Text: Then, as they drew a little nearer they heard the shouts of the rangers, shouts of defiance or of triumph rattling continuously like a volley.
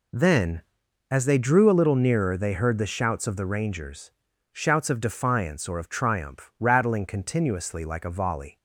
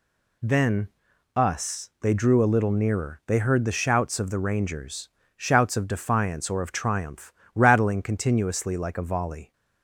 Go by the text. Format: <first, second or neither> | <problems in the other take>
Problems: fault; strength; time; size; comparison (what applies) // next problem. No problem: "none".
first | says "us" for "as"; at 1.3 s // pauses between "triumph" and "rattling"; slight; at 7.3 s; 0.22 s long